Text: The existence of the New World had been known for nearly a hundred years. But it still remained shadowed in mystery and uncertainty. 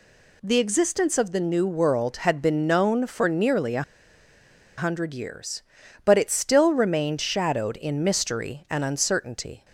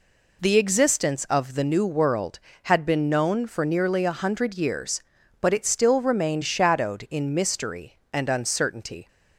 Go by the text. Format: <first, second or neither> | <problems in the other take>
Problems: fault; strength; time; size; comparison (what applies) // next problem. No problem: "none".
second | pauses between "a" and "hundred"; noticeable; at 3.8 s; 0.96 s long